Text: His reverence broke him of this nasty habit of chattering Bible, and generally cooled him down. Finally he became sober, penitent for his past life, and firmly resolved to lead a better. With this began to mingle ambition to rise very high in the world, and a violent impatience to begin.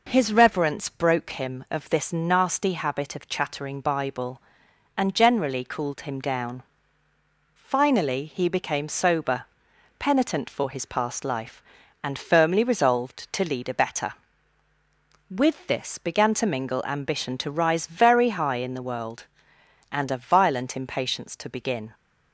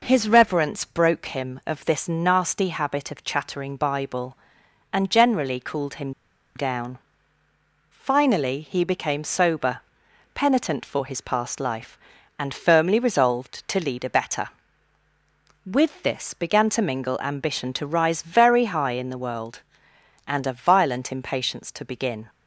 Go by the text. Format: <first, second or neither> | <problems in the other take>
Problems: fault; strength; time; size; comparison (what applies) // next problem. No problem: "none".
first | pauses between "him" and "down"; at 6.1 s; 0.44 s long